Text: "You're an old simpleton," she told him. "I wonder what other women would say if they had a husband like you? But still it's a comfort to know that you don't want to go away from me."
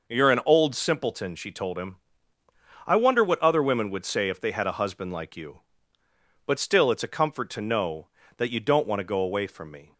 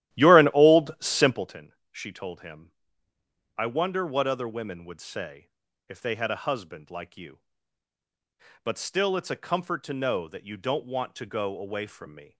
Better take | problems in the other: first | starts louder than the rest; strong; until 1.6 s; 13.5 dB // pauses between "say" and "if"; at 5.4 s; 0.40 s long

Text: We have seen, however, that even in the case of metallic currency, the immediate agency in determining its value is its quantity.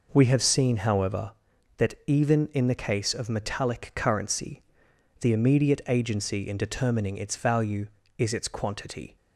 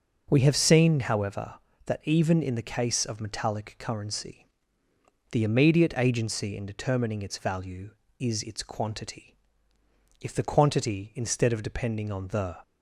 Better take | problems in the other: first | goes on to say "If the quantity instead of depending on the"; strong; from 10.2 s on; 2.3 s long

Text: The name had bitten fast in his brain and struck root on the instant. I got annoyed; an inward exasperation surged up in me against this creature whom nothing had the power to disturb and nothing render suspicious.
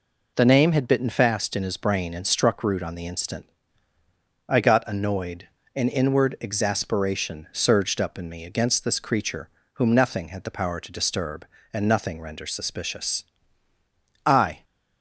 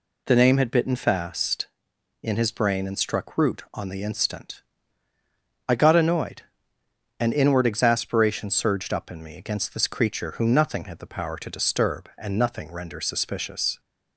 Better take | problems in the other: second | pauses between "creature" and "whom"; slight; at 9.4 s; 0.26 s long // goes on to say "I"; slight; from 14.2 s on; 0.38 s long

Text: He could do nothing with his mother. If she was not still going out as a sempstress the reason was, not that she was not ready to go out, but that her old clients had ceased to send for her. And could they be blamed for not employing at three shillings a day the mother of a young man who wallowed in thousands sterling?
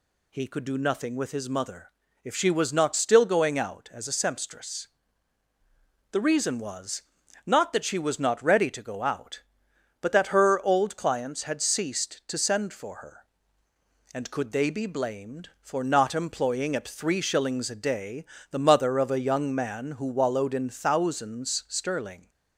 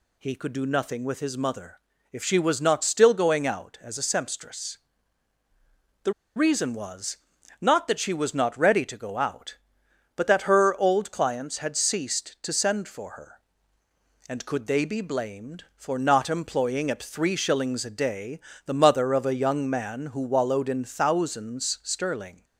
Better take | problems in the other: first | pauses between "sempstress" and "the"; strong; at 4.7 s; 1.2 s long; strong in the first // pauses between "the" and "reason"; slight; at 6.1 s; 0.22 s long // pauses between "day" and "the"; slight; at 18.3 s; 0.26 s long; slight in the first

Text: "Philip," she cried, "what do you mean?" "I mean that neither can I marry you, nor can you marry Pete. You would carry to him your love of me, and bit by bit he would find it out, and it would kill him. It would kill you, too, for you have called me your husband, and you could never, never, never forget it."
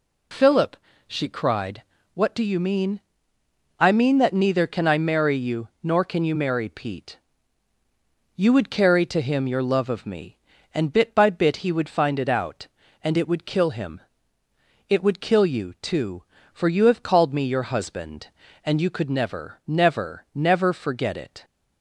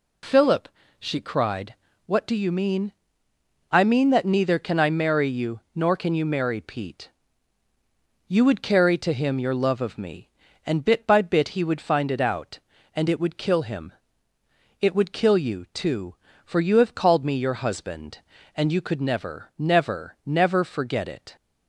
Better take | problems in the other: neither | none

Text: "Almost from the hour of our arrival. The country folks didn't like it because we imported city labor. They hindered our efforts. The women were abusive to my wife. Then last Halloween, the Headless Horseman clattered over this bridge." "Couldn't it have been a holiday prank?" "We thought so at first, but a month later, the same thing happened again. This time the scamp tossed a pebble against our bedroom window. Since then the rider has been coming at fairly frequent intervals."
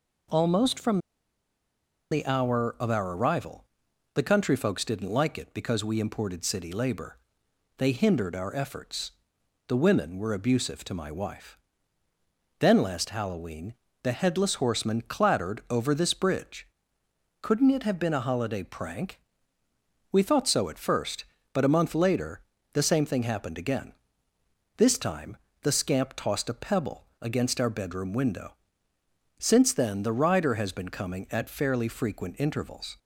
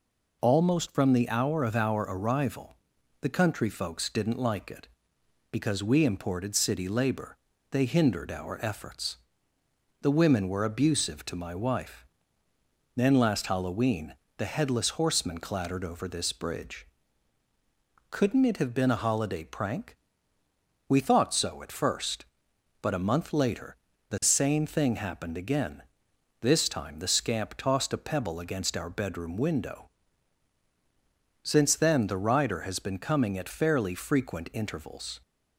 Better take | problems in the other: second | pauses between "from" and "the"; at 0.9 s; 1.1 s long // pauses between "time" and "the"; slight; at 25.3 s; 0.24 s long // pauses between "pebble" and "against"; slight; at 27.0 s; 0.16 s long

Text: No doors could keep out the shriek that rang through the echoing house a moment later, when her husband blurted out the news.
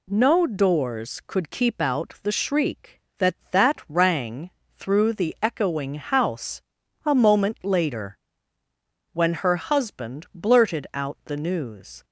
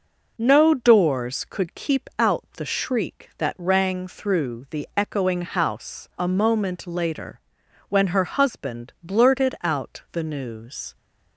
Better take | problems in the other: second | says "that" twice; at 3.5 s // pauses between "rang" and "through"; slight; at 4.4 s; 0.30 s long // pauses between "house" and "a"; at 6.6 s; 0.42 s long

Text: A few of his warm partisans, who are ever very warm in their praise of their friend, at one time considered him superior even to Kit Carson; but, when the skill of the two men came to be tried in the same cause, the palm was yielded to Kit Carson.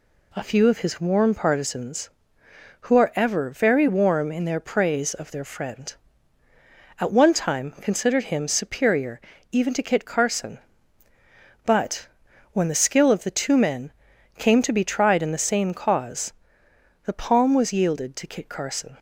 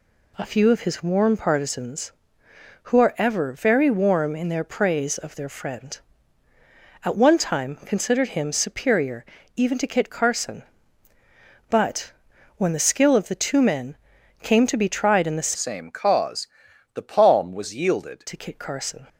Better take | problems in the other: first | pauses between "superior" and "even"; slight; at 9.2 s; 0.30 s long; slight in the first // pauses between "men" and "came"; noticeable; at 13.9 s; 0.48 s long; noticeable in the first // changes voice from "same" to "yielded"; from 15.5 to 18.2 s; 2.7 s long

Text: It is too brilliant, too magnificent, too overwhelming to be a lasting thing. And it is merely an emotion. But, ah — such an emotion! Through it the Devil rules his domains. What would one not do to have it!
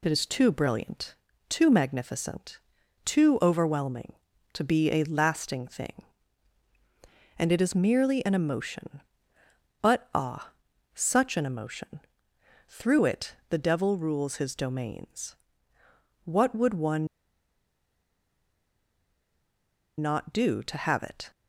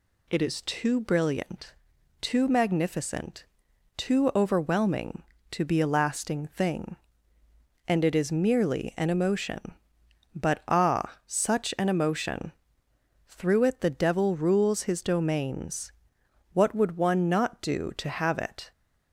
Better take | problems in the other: second | pauses between "one" and "not"; strong; at 17.0 s; 2.9 s long

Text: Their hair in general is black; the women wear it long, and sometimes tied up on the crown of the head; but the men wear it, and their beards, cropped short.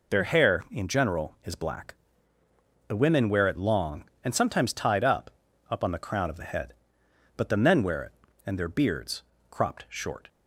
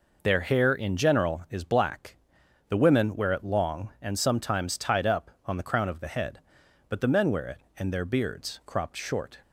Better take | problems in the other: second | says "up" twice; at 5.6 s

